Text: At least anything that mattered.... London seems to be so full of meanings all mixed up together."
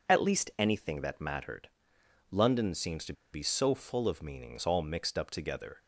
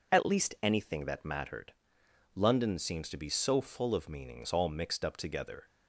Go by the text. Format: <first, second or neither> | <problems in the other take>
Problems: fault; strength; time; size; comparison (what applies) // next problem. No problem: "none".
second | pauses between "to" and "be"; slight; at 3.1 s; 0.20 s long